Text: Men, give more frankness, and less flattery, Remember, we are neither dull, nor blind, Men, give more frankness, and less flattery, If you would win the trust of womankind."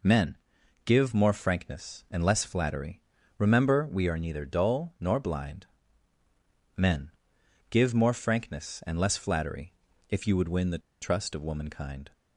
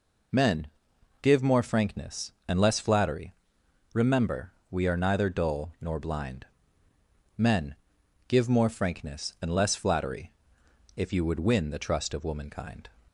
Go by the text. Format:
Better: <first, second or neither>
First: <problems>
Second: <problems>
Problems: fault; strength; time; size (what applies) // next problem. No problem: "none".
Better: second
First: pauses between "the" and "trust"; slight; at 10.8 s; 0.23 s long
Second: none